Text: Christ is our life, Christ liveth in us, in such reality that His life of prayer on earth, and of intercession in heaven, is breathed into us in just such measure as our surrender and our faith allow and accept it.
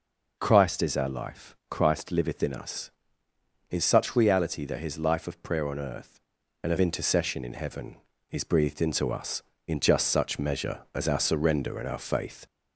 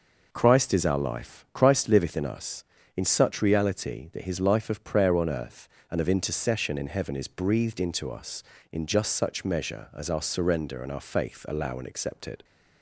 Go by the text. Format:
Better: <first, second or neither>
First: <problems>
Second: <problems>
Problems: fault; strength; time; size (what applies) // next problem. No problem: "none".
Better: second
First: stops before "allow and accept it"; at 12.4 s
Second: none